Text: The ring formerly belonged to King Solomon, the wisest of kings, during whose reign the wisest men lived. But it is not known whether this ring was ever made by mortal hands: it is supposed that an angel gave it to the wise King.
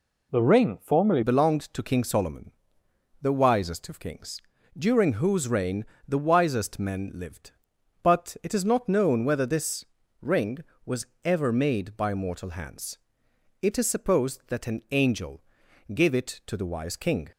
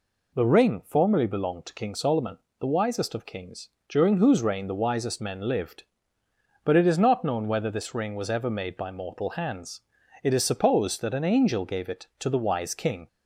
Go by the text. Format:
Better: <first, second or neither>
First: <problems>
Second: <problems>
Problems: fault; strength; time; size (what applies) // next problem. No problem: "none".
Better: second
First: changes voice at "belonged"; from 1.2 s on; 16.1 s long // pauses between "reign" and "the"; slight; at 5.8 s; 0.20 s long // pauses between "this" and "ring"; slight; at 9.8 s; 0.34 s long // pauses between "was" and "ever"; slight; at 11.0 s; 0.18 s long // pauses between "angel" and "gave"; noticeable; at 15.4 s; 0.54 s long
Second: none